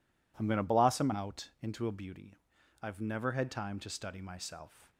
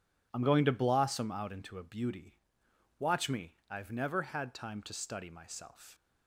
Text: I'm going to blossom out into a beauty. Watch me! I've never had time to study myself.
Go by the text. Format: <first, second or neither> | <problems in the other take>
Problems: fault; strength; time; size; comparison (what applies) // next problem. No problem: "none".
second | skips "Watch me"; at 2.5 s